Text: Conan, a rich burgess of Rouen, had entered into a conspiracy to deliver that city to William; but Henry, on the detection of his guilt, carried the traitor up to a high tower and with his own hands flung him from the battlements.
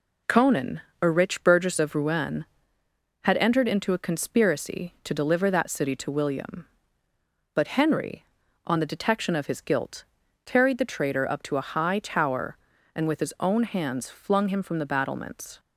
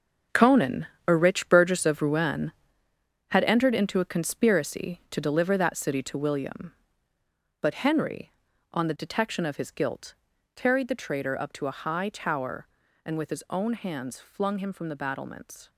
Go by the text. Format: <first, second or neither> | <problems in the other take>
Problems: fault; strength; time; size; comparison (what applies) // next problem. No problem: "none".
first | gets quieter; strong; throughout; 11 dB